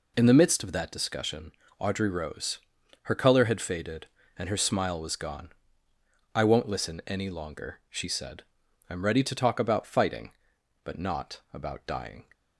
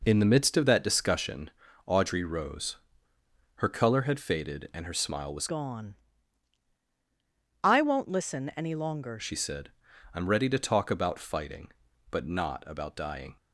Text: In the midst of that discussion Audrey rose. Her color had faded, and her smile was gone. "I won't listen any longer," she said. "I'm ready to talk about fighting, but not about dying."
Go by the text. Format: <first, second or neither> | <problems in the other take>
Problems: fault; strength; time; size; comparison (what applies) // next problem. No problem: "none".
first | pauses between "discussion" and "Audrey"; at 1.4 s; 0.38 s long; slight in the first // changes voice from "gone" to "longer"; from 5.4 to 9.1 s; 3.7 s long